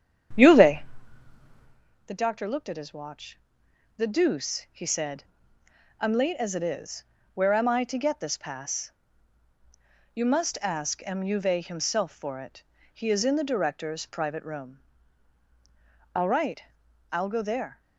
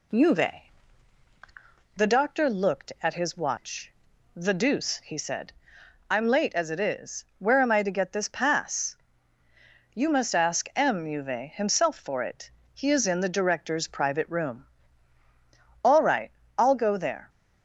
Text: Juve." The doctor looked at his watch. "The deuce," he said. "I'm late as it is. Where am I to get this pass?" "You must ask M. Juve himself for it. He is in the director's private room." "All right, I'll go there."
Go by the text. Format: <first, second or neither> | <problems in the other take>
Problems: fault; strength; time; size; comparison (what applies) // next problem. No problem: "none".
second | starts louder than the rest; strong; until 1.9 s; 9 dB